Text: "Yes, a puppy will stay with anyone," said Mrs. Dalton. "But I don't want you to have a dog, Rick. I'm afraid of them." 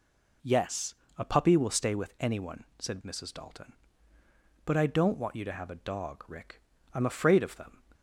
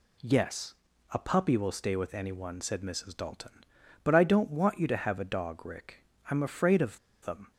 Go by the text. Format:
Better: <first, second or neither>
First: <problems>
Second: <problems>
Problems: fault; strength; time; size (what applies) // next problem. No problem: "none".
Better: first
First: none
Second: pauses between "of" and "them"; slight; at 6.9 s; 0.23 s long